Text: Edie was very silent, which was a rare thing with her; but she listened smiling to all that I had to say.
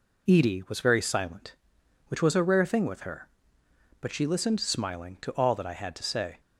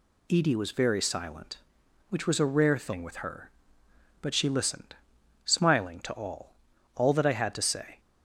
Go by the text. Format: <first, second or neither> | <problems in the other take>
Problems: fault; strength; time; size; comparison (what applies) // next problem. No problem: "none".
first | pauses between "listened" and "smiling"; noticeable; at 4.9 s; 0.50 s long // says "all" twice; at 6.9 s